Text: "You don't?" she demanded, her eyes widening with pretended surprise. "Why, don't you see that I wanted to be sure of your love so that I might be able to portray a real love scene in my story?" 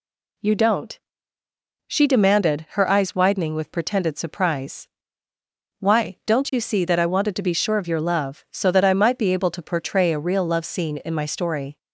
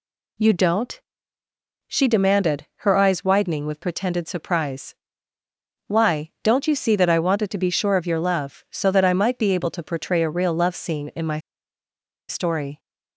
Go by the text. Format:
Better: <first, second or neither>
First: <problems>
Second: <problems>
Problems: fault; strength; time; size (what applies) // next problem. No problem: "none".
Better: first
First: none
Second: pauses between "my" and "story"; noticeable; at 11.3 s; 0.89 s long